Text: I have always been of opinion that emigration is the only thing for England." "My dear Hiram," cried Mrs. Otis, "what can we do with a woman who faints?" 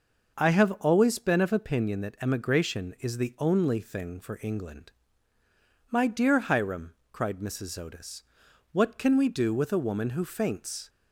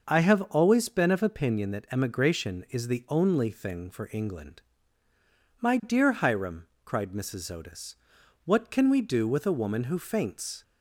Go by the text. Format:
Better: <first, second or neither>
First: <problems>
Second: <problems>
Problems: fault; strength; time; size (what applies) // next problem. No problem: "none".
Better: neither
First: none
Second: none